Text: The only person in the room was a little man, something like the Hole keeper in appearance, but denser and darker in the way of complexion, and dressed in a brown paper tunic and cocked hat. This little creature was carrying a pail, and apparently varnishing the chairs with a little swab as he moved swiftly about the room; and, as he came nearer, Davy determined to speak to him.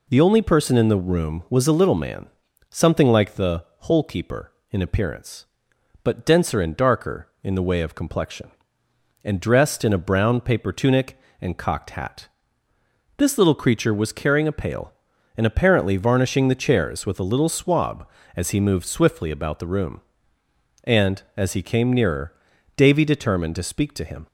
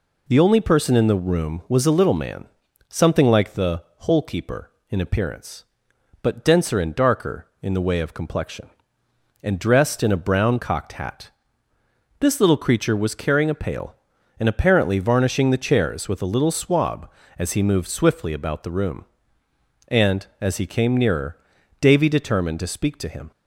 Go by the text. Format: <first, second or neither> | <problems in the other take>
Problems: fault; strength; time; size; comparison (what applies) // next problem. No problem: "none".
first | pauses between "the" and "Hole"; slight; at 3.8 s; 0.18 s long; slight in the first // skips "paper tunic and"; at 10.5 s